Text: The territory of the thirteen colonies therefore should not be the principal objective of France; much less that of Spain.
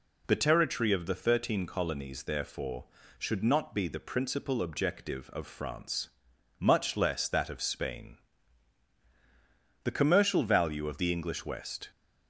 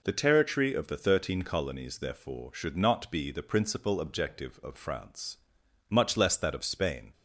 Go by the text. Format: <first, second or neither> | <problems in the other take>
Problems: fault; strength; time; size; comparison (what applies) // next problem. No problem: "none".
second | goes on to say "The commercial value of the English West"; strong; from 9.8 s on; 2.0 s long